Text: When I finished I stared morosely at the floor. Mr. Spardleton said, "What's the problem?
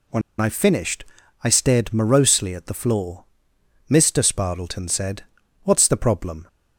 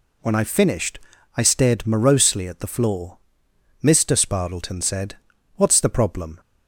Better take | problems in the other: second | pauses between "When" and "I"; slight; at 0.2 s; 0.18 s long // pauses between "finished" and "I"; at 1.0 s; 0.38 s long; also in the second

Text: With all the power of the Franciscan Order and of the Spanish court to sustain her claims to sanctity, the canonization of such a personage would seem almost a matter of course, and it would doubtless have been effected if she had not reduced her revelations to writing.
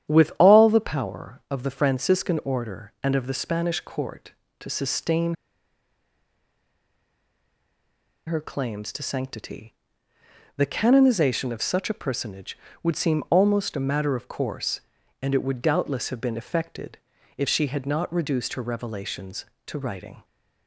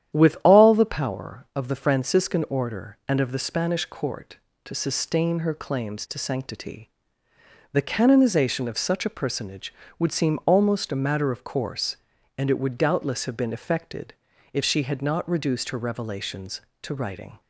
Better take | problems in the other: second | starts louder than the rest; strong; until 1.1 s; 10 dB; strong in the second // pauses between "sustain" and "her"; strong; at 5.3 s; 2.9 s long // pauses between "effected" and "if"; at 16.9 s; 0.40 s long; also in the second

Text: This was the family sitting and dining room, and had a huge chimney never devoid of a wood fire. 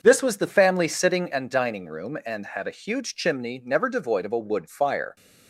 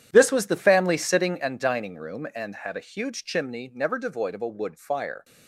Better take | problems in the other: first | gets quieter; strong; throughout; 14 dB // starts louder than the rest; strong; until 1.1 s; 10 dB; also in the first

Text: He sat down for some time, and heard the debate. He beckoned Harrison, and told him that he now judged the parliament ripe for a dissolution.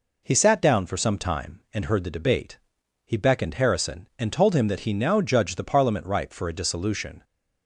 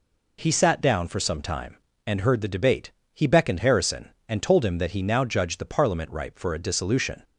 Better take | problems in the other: neither | none

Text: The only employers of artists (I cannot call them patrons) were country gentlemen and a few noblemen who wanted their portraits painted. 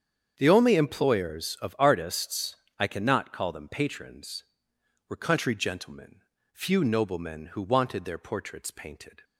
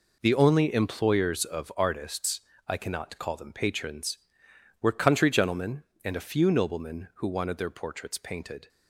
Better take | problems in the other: second | starts louder than the rest; strong; until 1.3 s; 7.5 dB // skips "and a"; at 6.3 s

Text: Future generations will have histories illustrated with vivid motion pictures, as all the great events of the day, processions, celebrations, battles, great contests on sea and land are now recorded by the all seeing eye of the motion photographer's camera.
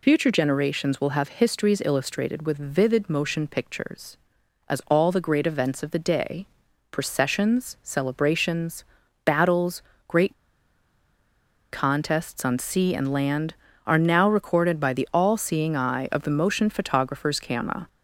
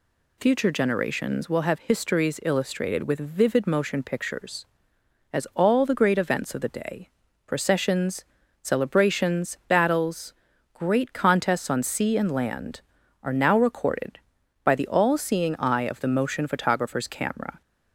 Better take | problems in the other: second | pauses between "great" and "contests"; strong; at 10.3 s; 1.3 s long

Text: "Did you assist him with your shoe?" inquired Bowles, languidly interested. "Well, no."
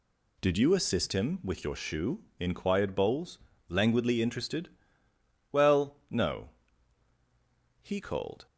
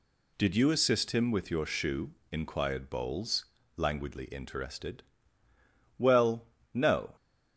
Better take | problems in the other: second | goes on to say "He called"; noticeable; from 7.8 s on; 0.64 s long

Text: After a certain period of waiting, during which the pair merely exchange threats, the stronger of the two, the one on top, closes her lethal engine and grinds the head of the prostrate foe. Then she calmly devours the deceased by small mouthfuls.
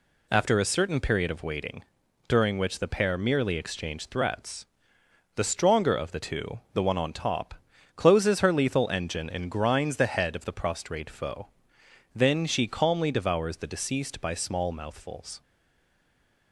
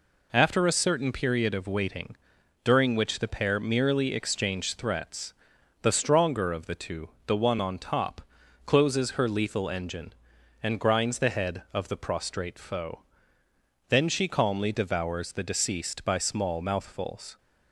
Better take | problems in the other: second | stays silent after the last word; from 15.4 s on; 1.1 s long

